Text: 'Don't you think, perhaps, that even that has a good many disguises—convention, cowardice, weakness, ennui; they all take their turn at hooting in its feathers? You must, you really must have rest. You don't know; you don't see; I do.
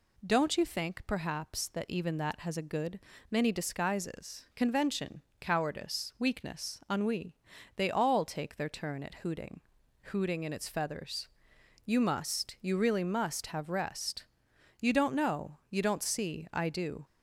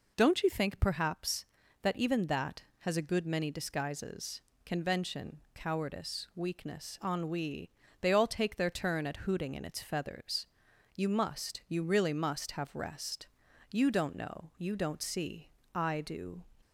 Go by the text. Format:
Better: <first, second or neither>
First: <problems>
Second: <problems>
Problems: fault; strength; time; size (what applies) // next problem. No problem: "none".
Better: second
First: pauses between "good" and "many"; slight; at 2.9 s; 0.30 s long // says "hooting" twice; at 10.0 s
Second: none